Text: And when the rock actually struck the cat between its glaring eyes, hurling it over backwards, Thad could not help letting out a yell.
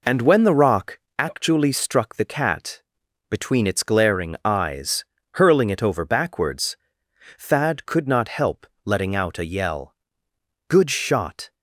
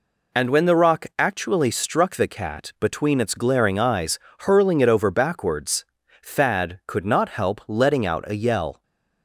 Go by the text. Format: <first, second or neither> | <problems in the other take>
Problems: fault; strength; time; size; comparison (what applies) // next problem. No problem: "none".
second | pauses between "rock" and "actually"; slight; at 0.9 s; 0.20 s long // pauses between "cat" and "between"; noticeable; at 2.8 s; 0.48 s long // pauses between "help" and "letting"; slight; at 8.6 s; 0.18 s long // goes on to say "Good shot"; noticeable; from 10.6 s on; 0.86 s long